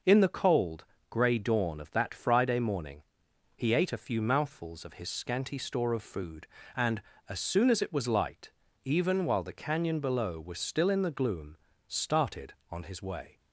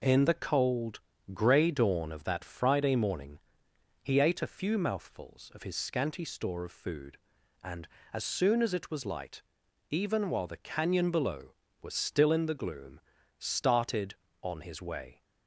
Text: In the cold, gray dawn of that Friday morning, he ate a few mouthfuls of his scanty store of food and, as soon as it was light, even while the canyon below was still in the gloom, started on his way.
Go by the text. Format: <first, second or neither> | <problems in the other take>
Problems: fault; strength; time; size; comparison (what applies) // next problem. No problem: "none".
neither | none